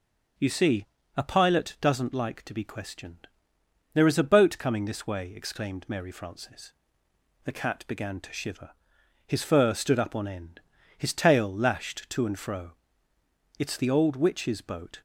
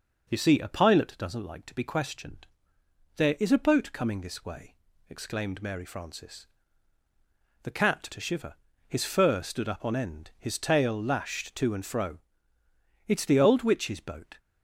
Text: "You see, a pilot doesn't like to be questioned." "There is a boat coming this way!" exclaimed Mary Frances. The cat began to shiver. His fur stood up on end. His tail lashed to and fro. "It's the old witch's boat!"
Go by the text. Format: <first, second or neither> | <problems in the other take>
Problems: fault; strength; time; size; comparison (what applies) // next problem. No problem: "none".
first | skips "began"; at 8.0 s